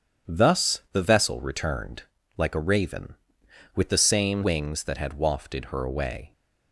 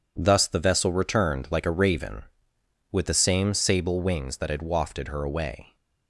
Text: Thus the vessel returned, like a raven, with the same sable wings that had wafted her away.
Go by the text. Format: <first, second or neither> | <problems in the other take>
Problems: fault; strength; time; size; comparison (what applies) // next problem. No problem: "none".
second | starts louder than the rest; strong; until 1.3 s; 8.5 dB // skips "sable"; at 4.4 s